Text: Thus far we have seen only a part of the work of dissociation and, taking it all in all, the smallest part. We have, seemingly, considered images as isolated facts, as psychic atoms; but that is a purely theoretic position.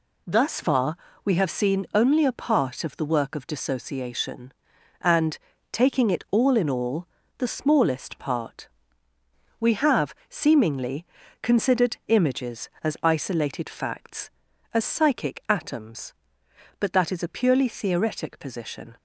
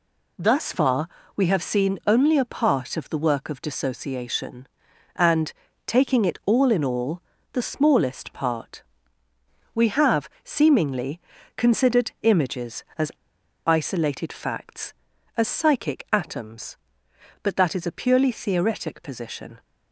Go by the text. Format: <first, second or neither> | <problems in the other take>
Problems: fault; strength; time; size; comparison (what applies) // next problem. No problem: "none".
first | pauses between "far" and "we"; slight; at 1.0 s; 0.28 s long; slight in the first // pauses between "as" and "isolated"; noticeable; at 13.1 s; 0.54 s long